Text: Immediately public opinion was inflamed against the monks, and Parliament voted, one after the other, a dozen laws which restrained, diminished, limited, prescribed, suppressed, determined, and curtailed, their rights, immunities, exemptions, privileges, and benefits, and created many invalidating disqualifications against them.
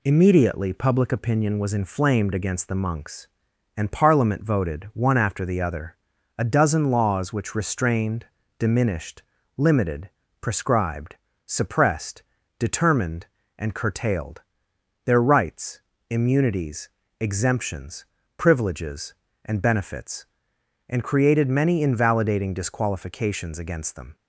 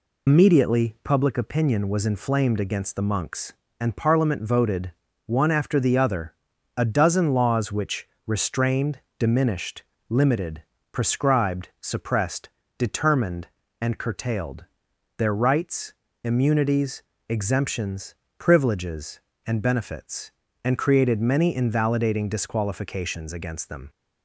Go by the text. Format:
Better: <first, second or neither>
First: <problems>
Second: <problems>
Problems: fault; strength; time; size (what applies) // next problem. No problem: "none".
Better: first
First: none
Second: loses the start of "Immediately"; at 0.2 s; 90 ms // pauses between "which" and "restrained"; slight; at 8.0 s; 0.18 s long